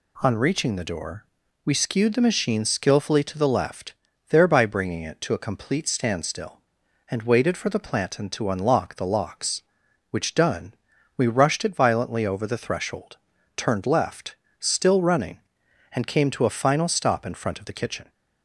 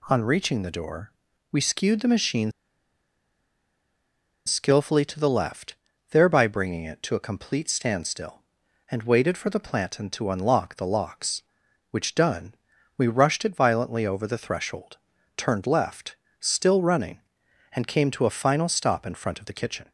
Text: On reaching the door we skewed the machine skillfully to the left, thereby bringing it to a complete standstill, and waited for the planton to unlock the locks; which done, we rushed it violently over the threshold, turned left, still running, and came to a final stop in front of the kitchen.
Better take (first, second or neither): first